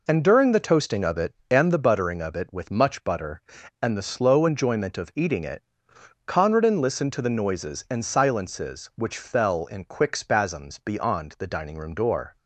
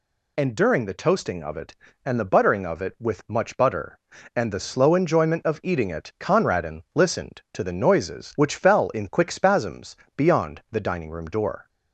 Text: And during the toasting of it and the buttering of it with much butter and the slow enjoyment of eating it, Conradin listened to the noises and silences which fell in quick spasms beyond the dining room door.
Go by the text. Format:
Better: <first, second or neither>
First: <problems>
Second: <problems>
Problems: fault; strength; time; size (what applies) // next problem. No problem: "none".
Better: first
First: none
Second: skips "and silences"; at 8.3 s // pauses between "spasms" and "beyond"; slight; at 9.9 s; 0.22 s long